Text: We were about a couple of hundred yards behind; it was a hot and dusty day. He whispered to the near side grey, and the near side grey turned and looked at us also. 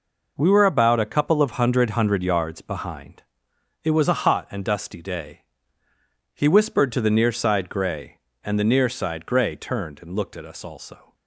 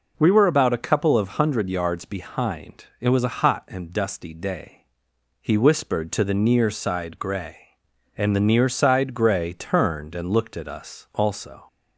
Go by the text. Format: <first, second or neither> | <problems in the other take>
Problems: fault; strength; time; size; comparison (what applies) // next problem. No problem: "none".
second | says "hundred" twice; at 1.9 s